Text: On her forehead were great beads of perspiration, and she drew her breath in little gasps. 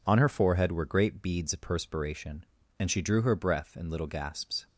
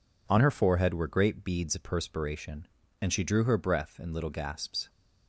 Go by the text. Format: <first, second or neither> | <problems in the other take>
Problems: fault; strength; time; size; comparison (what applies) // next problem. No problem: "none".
neither | none